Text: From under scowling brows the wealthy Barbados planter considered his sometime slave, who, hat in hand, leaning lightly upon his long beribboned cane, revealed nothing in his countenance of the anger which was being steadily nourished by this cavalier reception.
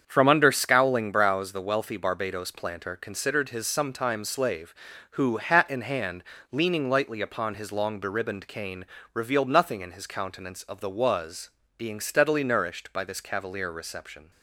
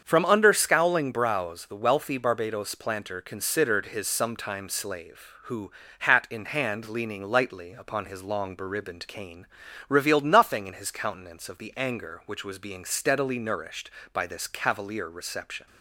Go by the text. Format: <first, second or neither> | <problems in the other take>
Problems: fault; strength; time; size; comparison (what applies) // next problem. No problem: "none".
second | starts louder than the rest; strong; until 1.0 s; 7.5 dB; strong in the second // skips "anger which"; at 10.9 s // pauses between "was" and "being"; slight; at 11.5 s; 0.26 s long